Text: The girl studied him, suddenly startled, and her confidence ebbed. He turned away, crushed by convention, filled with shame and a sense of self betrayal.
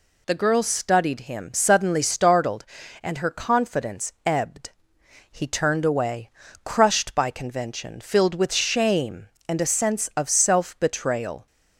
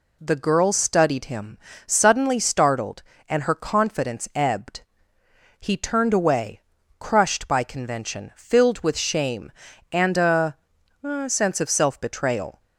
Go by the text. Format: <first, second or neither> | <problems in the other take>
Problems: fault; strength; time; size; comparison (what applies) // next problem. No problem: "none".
first | says "a" twice; at 11.0 s